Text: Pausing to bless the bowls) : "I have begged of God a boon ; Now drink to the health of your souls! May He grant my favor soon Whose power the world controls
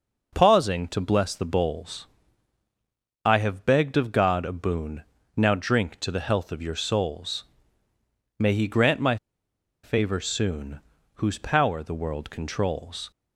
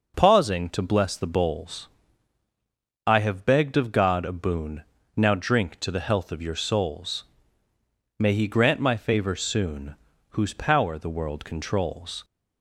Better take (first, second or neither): second